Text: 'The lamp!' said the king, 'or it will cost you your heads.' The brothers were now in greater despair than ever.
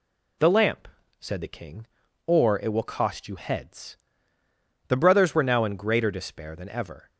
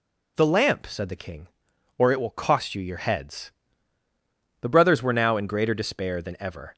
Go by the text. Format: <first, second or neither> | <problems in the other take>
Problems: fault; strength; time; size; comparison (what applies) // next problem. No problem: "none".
second | skips "your"; at 3.3 s